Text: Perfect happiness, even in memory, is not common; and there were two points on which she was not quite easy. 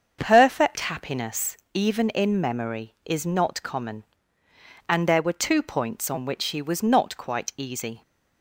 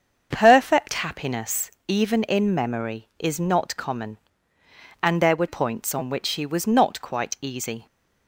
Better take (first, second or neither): first